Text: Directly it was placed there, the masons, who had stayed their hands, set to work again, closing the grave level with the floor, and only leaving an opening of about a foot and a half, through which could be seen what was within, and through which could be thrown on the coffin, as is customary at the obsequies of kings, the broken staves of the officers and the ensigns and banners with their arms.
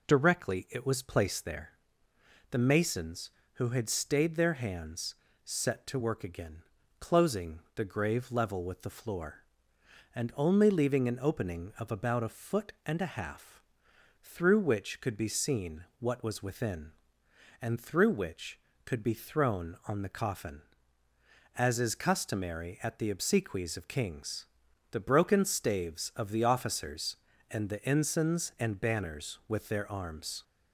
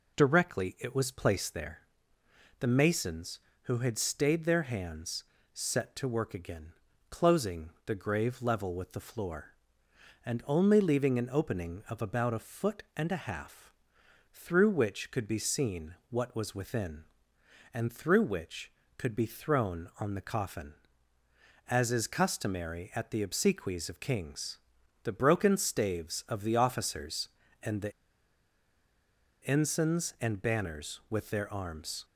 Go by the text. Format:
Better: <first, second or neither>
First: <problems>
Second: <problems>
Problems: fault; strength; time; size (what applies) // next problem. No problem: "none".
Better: first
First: pauses between "closing" and "the"; slight; at 7.5 s; 0.16 s long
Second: pauses between "closing" and "the"; slight; at 7.6 s; 0.16 s long // pauses between "the" and "ensigns"; strong; at 27.9 s; 1.5 s long